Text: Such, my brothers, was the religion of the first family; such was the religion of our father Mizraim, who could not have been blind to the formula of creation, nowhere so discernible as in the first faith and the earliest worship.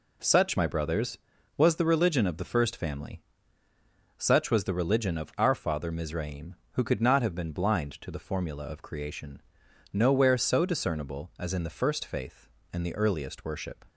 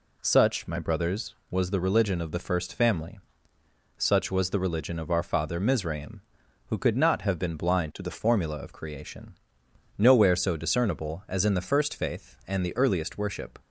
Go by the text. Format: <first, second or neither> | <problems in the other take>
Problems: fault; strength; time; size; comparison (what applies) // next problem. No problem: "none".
first | changes voice from "to" to "the"; from 7.9 to 8.1 s; 0.2 s long